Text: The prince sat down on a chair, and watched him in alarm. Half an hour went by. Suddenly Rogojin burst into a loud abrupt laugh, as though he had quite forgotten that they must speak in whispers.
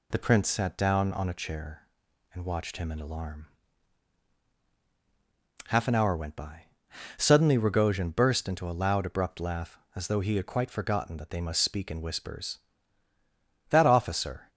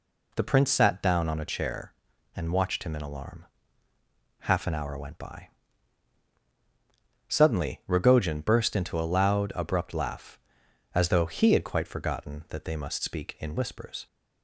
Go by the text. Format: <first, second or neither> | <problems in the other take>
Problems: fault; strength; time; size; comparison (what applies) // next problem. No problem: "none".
second | goes on to say "That officer"; noticeable; from 13.6 s on; 0.80 s long